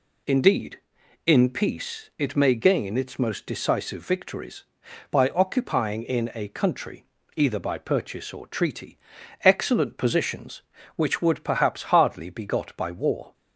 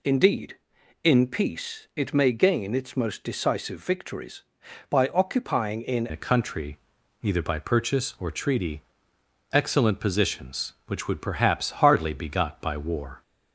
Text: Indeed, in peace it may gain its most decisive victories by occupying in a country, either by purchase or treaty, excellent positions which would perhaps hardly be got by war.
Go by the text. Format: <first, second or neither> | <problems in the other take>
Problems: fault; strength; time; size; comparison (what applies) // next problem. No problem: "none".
first | changes voice at "a"; from 6.1 s on; 7.1 s long